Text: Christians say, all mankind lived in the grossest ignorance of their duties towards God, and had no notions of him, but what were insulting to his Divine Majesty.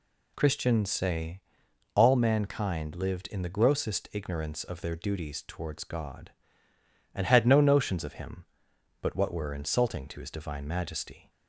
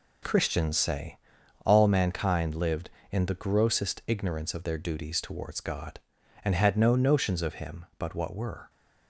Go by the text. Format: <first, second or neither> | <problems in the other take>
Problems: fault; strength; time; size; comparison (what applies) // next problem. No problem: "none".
first | stops before "insulting to his Divine Majesty"; at 8.6 s